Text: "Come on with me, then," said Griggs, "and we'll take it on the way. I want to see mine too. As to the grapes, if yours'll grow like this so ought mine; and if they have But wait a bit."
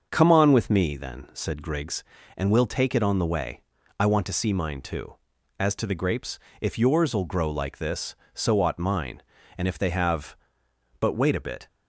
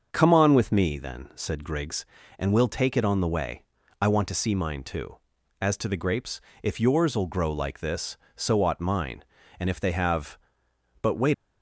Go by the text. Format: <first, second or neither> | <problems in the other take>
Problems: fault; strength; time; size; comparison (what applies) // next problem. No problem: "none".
first | starts louder than the rest; until 1.1 s; 6.5 dB; also in the first // stops before "a bit"; at 11.3 s